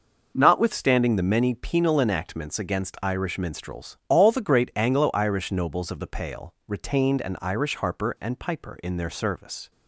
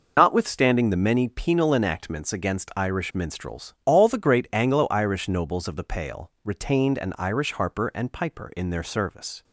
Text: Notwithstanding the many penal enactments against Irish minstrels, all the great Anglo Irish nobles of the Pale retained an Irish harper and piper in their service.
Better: first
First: none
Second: loses the start of "Notwithstanding"; at 0.1 s; 85 ms

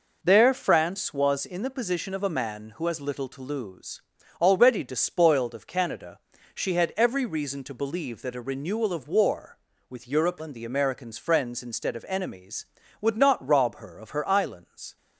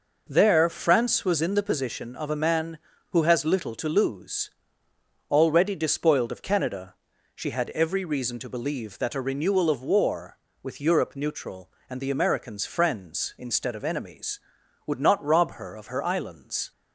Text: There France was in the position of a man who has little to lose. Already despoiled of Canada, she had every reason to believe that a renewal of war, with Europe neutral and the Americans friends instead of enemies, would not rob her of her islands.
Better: second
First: skips "neutral"; at 10.4 s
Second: none

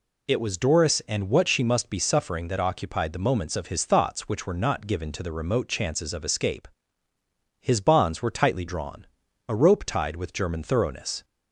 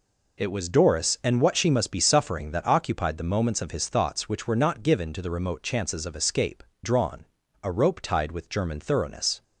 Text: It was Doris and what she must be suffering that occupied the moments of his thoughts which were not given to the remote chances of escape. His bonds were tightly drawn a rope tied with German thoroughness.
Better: first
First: pauses between "drawn" and "a"; at 9.0 s; 0.42 s long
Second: skips "His bonds were tightly"; at 6.7 s // pauses between "drawn" and "a"; slight; at 7.2 s; 0.36 s long

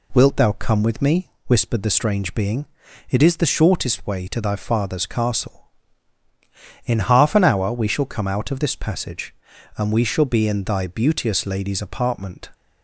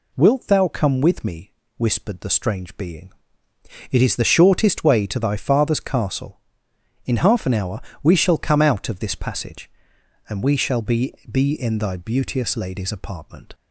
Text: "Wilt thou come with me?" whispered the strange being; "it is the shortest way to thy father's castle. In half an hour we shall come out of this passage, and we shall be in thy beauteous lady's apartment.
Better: first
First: none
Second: pauses between "hour" and "we"; slight; at 7.8 s; 0.22 s long // says "be" twice; at 11.3 s

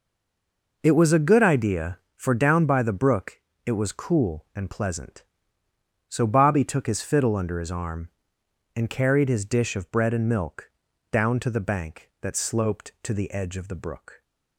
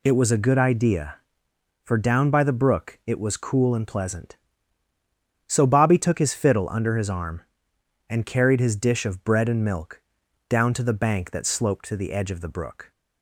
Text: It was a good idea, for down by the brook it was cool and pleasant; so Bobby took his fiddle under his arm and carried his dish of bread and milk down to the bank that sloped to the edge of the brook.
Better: second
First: stays silent before the first word; slight; until 0.8 s; 0.8 s long // pauses between "brook" and "it"; slight; at 3.4 s; 0.24 s long // pauses between "milk" and "down"; at 10.7 s; 0.40 s long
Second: pauses between "milk" and "down"; noticeable; at 10.0 s; 0.48 s long

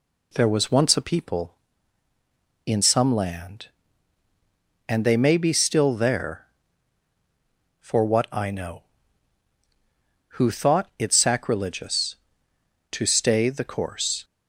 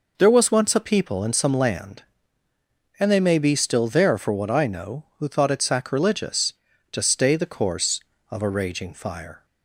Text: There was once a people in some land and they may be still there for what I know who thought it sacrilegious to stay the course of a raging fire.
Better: second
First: stops before "of a raging fire"; at 14.2 s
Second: none

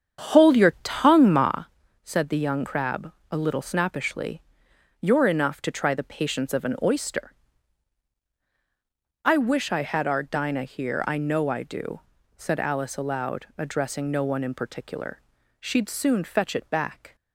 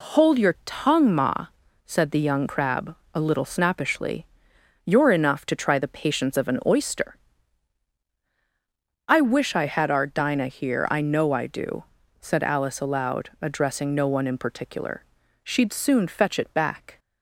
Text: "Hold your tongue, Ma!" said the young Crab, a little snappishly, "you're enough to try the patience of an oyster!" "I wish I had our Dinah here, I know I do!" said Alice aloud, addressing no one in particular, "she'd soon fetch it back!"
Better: second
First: starts louder than the rest; strong; until 1.7 s; 8 dB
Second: none

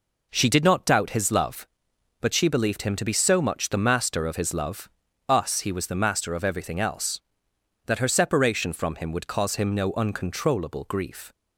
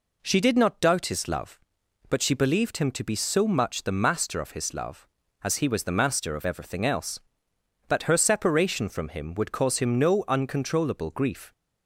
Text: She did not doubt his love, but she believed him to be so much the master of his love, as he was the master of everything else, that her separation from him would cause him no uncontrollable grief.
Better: second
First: says "us" for "as"; at 5.2 s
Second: none

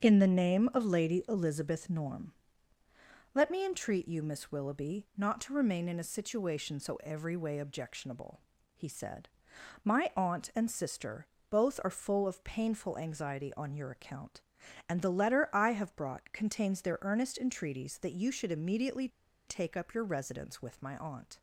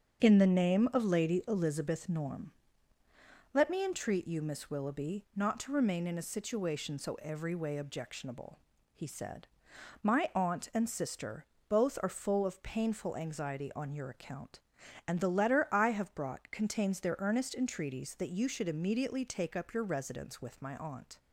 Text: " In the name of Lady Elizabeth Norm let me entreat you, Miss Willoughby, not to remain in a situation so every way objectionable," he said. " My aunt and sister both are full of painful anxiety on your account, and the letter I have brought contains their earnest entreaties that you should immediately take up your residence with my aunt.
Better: second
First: starts louder than the rest; strong; until 1.0 s; 8.5 dB // pauses between "Norm" and "let"; at 2.3 s; 1.0 s long // pauses between "sister" and "both"; slight; at 11.2 s; 0.24 s long // pauses between "immediately" and "take"; at 19.0 s; 0.40 s long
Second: starts louder than the rest; strong; until 1.2 s; 8.5 dB // pauses between "Norm" and "let"; at 2.5 s; 1.0 s long // pauses between "sister" and "both"; slight; at 11.4 s; 0.24 s long

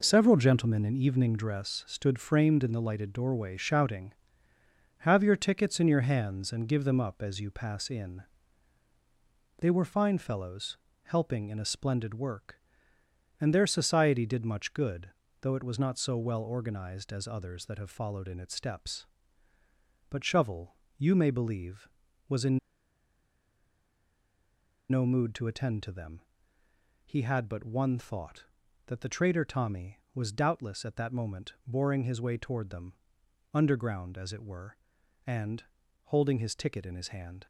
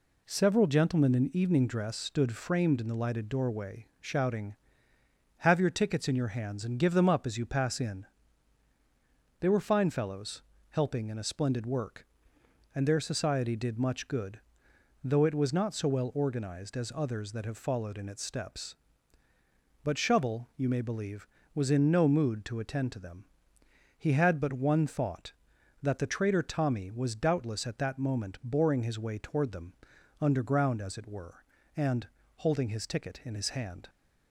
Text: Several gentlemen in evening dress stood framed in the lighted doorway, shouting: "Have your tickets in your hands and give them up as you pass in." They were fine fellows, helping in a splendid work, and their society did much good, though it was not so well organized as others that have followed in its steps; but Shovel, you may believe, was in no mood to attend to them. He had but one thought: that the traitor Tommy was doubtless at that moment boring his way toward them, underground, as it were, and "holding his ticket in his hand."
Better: second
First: pauses between "in" and "no"; strong; at 22.5 s; 2.3 s long // pauses between "and" and "holding"; at 35.6 s; 0.40 s long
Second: pauses between "and" and "holding"; slight; at 32.0 s; 0.30 s long

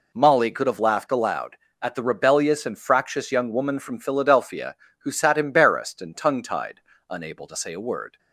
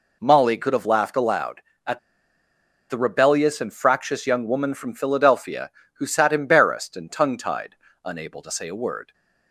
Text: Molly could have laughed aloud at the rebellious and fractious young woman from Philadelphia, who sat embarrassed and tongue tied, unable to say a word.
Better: first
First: none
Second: pauses between "at" and "the"; noticeable; at 1.9 s; 0.91 s long

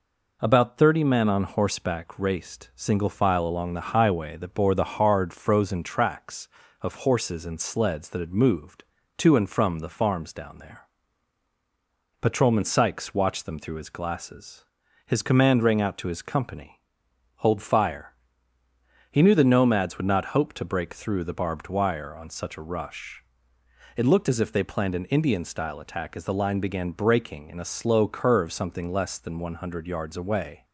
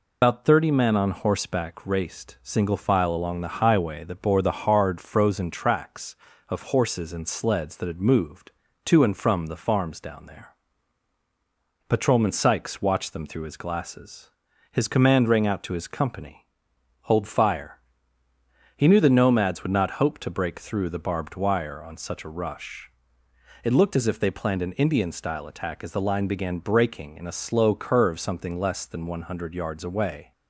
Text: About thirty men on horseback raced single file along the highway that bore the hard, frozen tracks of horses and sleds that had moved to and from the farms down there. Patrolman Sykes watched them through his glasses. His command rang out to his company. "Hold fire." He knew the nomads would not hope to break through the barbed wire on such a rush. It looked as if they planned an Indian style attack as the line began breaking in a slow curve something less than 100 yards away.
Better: first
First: none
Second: loses the start of "About"; at 0.2 s; 135 ms

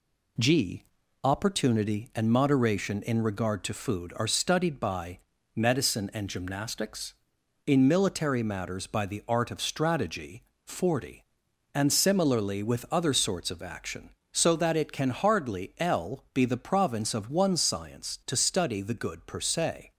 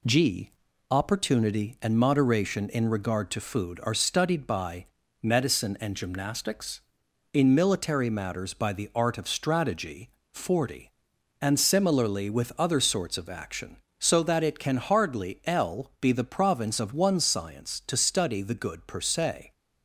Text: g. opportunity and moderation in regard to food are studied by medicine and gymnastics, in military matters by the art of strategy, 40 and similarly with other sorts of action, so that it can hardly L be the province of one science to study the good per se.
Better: neither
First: pauses between "by" and "medicine"; at 5.1 s; 0.38 s long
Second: pauses between "by" and "medicine"; at 4.8 s; 0.38 s long

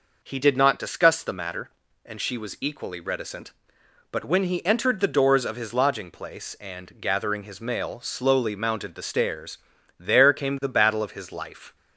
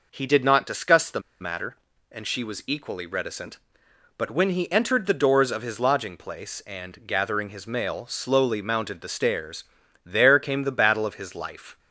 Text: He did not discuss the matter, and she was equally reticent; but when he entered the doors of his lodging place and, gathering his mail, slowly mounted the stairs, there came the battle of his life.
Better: first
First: none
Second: pauses between "the" and "matter"; slight; at 1.1 s; 0.21 s long

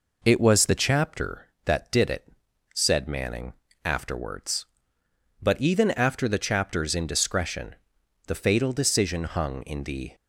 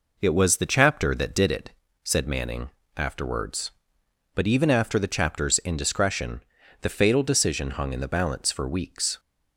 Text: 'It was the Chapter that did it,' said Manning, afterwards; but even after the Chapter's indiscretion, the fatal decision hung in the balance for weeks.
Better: second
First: stops before "balance for weeks"; at 10.1 s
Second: none

